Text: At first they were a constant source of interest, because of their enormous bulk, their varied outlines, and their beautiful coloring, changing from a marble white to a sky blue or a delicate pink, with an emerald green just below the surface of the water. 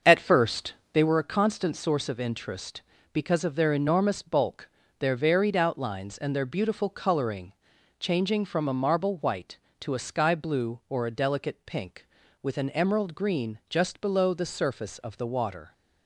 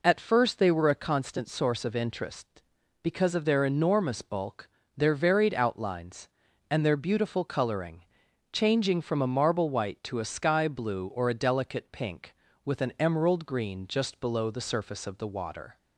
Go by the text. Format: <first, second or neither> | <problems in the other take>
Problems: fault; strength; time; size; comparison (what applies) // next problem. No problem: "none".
second | starts louder than the rest; until 1.2 s; 6.5 dB // pauses between "first" and "they"; slight; at 0.7 s; 0.20 s long